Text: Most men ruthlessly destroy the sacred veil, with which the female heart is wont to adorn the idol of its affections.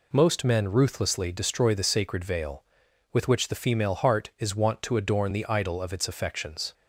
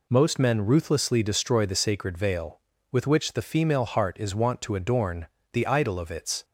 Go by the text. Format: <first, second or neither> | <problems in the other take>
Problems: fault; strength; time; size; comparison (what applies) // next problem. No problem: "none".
first | pauses between "adorn" and "the"; slight; at 5.2 s; 0.26 s long // stops before "affections"; at 6.4 s